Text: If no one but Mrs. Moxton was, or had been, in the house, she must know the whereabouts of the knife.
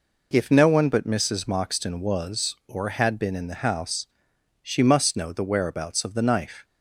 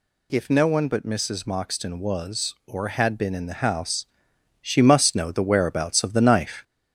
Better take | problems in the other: first | gets louder; slight; throughout; 3.5 dB

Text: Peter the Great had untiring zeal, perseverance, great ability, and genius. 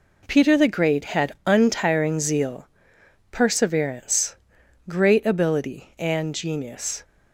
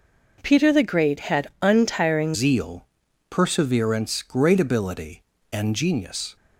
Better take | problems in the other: first | changes voice at "zeal"; from 2.3 s on; 4.0 s long

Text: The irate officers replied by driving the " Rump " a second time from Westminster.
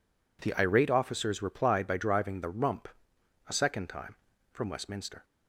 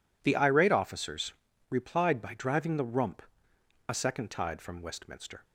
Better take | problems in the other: first | pauses between "officers" and "replied"; at 1.3 s; 0.38 s long // says "tide" for "time"; at 4.2 s

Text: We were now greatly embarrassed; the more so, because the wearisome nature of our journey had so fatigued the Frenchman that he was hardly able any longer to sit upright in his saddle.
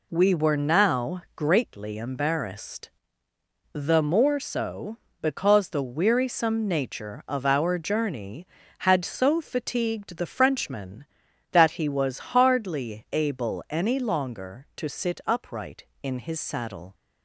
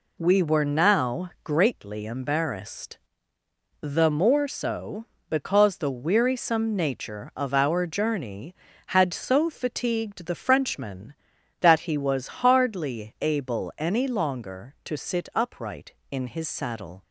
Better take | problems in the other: neither | none

